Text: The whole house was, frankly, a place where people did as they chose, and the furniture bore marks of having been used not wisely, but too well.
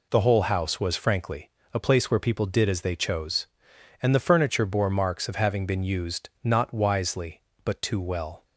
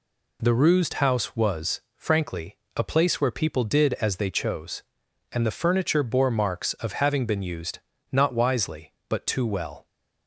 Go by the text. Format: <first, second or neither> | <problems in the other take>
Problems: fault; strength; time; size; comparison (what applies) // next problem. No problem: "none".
first | says "rused" for "whole"; at 0.5 s // pauses between "used" and "not"; slight; at 7.7 s; 0.34 s long